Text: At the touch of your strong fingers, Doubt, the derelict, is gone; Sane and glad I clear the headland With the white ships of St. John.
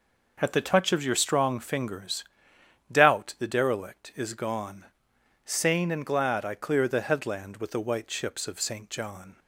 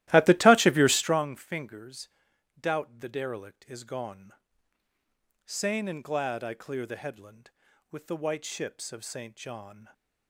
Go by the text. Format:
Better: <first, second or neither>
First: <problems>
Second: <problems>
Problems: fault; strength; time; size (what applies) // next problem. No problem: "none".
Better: first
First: none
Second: starts louder than the rest; strong; until 1.3 s; 15.5 dB